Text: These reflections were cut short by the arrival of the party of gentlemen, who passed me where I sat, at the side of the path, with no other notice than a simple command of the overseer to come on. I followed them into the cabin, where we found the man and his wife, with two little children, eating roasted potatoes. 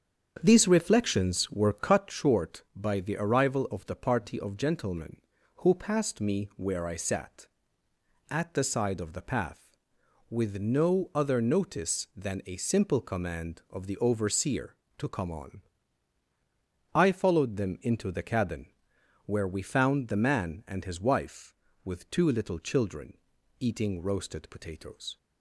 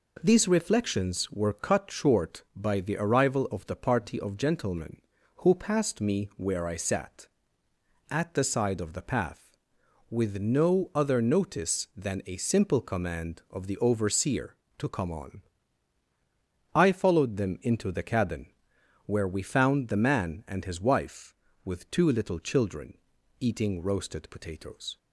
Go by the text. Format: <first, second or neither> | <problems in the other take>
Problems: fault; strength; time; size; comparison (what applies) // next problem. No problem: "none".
second | starts louder than the rest; strong; until 2.2 s; 7.5 dB